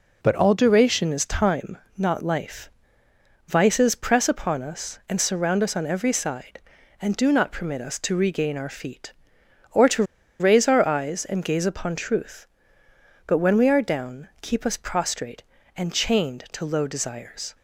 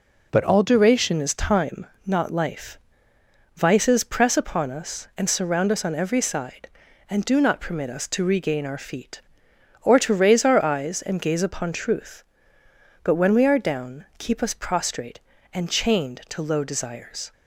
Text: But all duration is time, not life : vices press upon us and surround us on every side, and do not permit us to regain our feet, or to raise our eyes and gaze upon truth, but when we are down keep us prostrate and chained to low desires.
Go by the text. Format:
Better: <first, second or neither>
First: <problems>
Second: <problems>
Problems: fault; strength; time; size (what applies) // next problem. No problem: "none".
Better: second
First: pauses between "to" and "raise"; at 10.0 s; 0.36 s long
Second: none